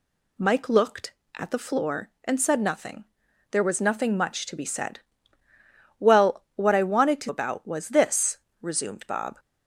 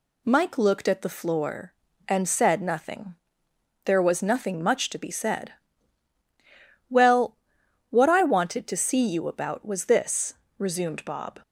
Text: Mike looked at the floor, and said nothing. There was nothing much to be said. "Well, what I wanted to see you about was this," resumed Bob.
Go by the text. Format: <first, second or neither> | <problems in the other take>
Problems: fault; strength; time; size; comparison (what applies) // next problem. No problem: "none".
second | skips "see you"; at 7.2 s